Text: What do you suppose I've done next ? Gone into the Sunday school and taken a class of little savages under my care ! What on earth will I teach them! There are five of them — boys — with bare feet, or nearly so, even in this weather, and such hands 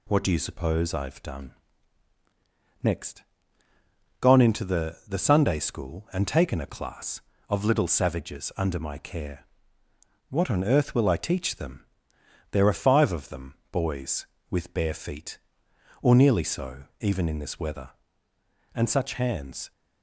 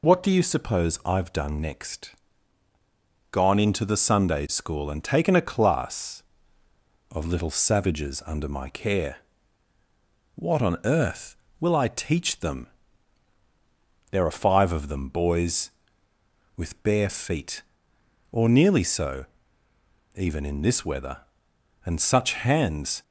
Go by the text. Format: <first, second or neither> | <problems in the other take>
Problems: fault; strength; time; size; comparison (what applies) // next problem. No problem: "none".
second | pauses between "done" and "next"; strong; at 1.5 s; 1.3 s long // says "the" twice; at 5.0 s